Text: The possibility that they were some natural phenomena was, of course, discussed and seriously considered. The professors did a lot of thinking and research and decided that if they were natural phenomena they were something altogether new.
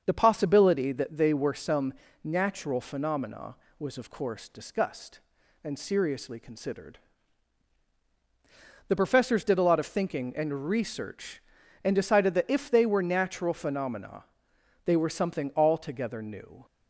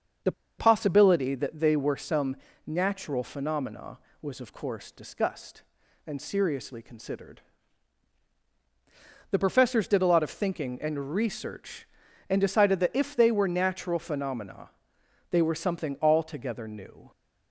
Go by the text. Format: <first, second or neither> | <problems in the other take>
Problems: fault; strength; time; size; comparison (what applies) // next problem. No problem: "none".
first | starts louder than the rest; until 1.5 s; 6.5 dB; also in the first // pauses between "The" and "possibility"; slight; at 0.3 s; 0.26 s long // pauses between "some" and "natural"; slight; at 2.3 s; 0.30 s long; slight in the first // pauses between "phenomena" and "they"; noticeable; at 14.6 s; 0.62 s long; noticeable in the first